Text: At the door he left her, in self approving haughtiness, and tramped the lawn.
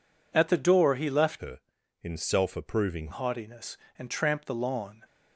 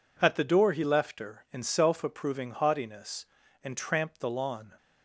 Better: second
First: changes voice from "her" to "approving"; from 1.3 to 3.0 s; 1.7 s long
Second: none

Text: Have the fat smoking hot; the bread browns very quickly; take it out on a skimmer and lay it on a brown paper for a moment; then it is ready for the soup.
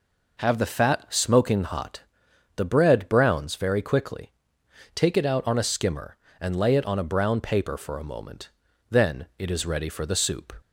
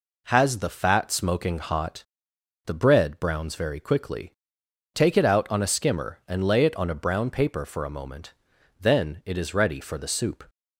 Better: first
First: none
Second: says "Has" for "Have"; at 0.2 s

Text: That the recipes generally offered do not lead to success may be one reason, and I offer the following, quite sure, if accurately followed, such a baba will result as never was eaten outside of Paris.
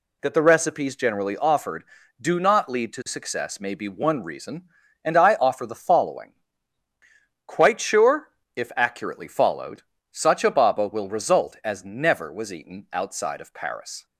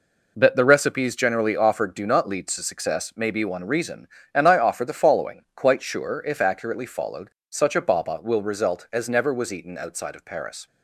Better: neither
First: none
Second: none

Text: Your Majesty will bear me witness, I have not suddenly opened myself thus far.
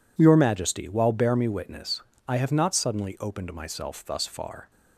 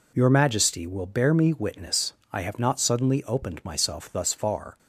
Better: second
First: says "while" for "will"; at 0.8 s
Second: none

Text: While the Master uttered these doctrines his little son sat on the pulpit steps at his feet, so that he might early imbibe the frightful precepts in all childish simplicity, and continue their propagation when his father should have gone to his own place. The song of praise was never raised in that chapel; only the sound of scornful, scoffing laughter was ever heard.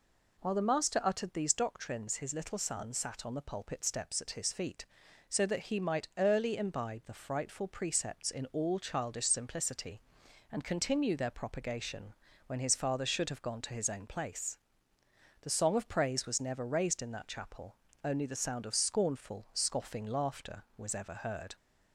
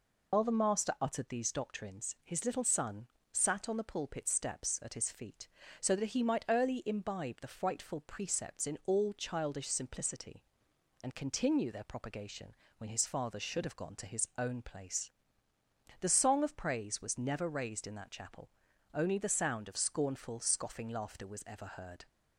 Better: first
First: pauses between "propagation" and "when"; slight; at 12.1 s; 0.32 s long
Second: loses the start of "While"; at 0.3 s; 85 ms // pauses between "son" and "sat"; slight; at 3.0 s; 0.26 s long // pauses between "propagation" and "when"; slight; at 12.5 s; 0.24 s long

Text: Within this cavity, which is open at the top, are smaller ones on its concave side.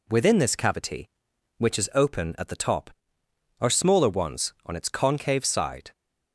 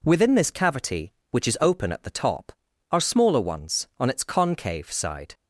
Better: neither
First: none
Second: none

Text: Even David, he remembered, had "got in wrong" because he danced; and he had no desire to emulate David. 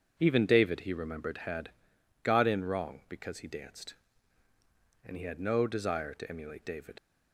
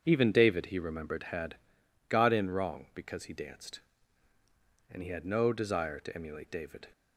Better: second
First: starts louder than the rest; until 1.1 s; 7 dB // pauses between "had" and "got"; noticeable; at 1.6 s; 0.54 s long // leaves "David" unfinished; at 6.9 s; 75 ms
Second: starts louder than the rest; strong; until 1.0 s; 7 dB // pauses between "had" and "got"; noticeable; at 1.5 s; 0.54 s long

